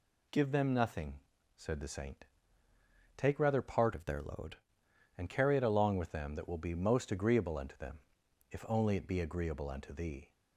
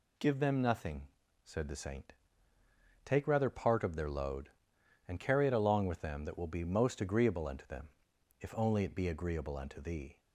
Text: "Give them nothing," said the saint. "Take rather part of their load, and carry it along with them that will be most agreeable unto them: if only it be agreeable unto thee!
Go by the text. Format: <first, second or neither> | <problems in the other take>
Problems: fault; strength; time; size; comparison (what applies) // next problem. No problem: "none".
second | changes voice from "of" to "load"; from 3.9 to 4.5 s; 0.6 s long